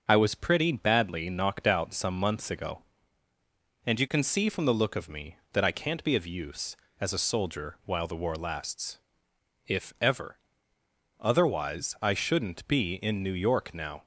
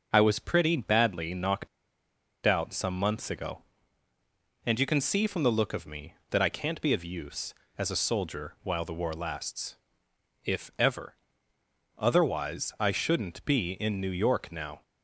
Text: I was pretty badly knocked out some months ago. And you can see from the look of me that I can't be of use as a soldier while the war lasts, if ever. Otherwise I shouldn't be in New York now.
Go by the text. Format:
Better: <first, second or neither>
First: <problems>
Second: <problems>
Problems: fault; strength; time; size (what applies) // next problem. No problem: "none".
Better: first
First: starts louder than the rest; until 1.0 s; 6.5 dB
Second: starts louder than the rest; until 1.1 s; 6.5 dB // pauses between "knocked" and "out"; noticeable; at 1.6 s; 0.78 s long